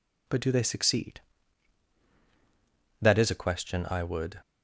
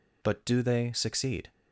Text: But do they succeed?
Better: second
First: goes on to say "That is a question I would"; from 3.0 s on; 1.4 s long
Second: none

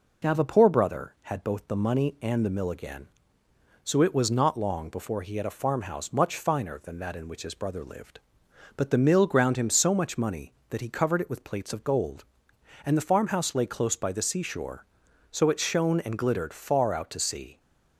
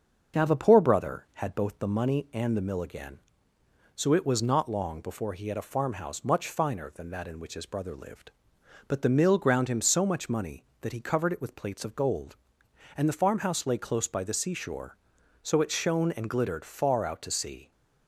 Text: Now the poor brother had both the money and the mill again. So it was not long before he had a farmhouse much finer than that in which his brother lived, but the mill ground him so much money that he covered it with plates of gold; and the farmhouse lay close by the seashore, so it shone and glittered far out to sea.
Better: first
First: none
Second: starts louder than the rest; until 1.9 s; 6.5 dB

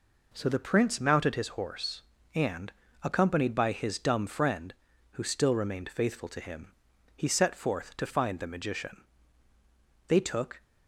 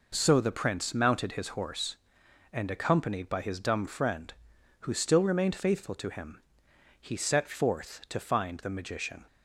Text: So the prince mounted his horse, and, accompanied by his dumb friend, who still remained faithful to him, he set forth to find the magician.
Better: second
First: goes on to say "They took"; from 10.0 s on; 0.54 s long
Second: none

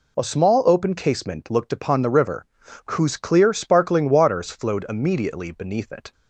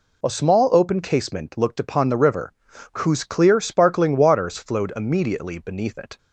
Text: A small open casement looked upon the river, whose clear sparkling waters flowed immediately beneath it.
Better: neither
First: none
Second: none

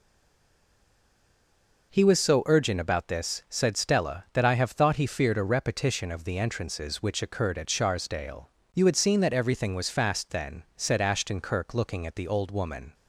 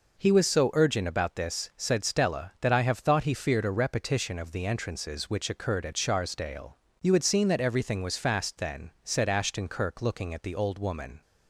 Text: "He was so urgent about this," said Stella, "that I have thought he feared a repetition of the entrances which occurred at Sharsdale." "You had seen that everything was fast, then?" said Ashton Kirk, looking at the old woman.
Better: second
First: stays silent before the first word; noticeable; until 1.9 s; 1.9 s long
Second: none

